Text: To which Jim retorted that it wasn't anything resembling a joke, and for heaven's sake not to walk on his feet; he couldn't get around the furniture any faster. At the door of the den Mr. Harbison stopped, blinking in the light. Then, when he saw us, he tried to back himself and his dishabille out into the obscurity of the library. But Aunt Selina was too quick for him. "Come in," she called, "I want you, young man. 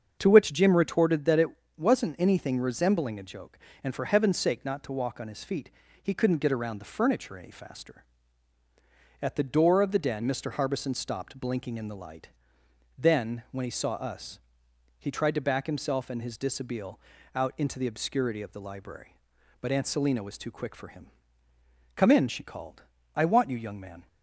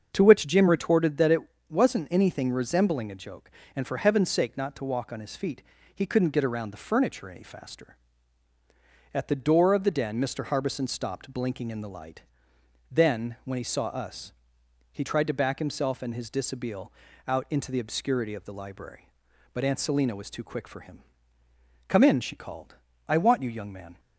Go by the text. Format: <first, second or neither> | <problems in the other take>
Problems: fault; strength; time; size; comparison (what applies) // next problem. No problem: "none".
neither | starts louder than the rest; the same in both // pauses between "it" and "wasn't"; slight; the same in both // pauses between "dishabille" and "out"; the same in both